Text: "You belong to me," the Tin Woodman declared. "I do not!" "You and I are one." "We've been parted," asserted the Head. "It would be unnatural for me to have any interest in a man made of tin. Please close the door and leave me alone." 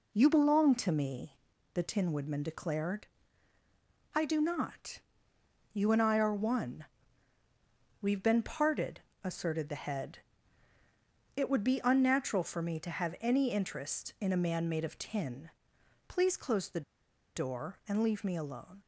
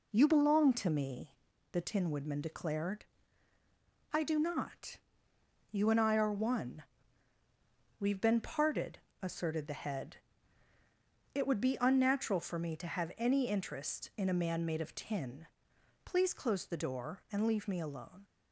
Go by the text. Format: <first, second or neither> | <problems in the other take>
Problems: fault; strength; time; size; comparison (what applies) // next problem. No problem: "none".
second | pauses between "the" and "door"; noticeable; at 16.8 s; 0.54 s long